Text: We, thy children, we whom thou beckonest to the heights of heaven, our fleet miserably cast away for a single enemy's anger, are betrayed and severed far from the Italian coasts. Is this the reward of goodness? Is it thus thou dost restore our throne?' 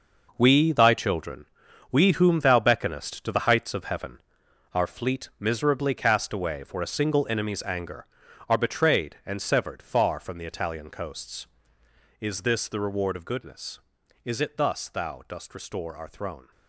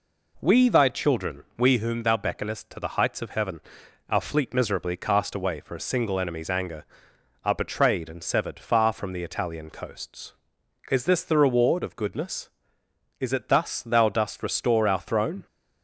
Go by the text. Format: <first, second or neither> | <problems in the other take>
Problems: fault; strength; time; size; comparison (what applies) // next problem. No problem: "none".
second | gets quieter; strong; throughout; 11 dB